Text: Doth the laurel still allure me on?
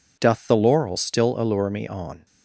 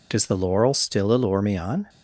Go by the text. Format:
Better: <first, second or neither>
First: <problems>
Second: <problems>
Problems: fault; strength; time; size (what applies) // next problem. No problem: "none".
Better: first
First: none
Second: says "Does" for "Doth"; at 0.1 s